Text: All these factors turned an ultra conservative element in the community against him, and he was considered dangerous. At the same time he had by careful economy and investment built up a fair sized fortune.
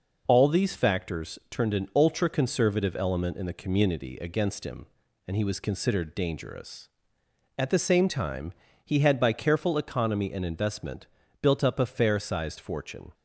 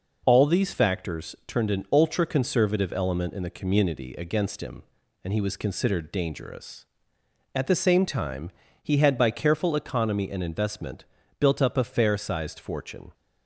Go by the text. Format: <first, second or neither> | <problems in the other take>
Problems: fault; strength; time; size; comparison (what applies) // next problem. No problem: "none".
neither | pauses between "time" and "he"; slight; the same in both // pauses between "investment" and "built"; the same in both